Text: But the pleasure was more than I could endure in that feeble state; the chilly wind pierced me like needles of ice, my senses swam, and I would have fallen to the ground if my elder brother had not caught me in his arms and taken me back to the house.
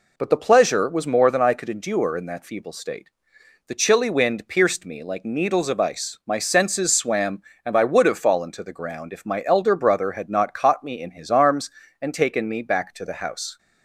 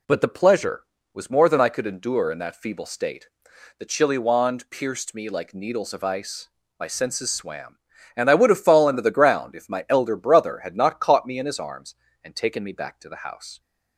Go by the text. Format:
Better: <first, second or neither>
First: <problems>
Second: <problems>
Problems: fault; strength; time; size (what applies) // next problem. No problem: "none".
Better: first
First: none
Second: says "wand" for "wind"; at 4.1 s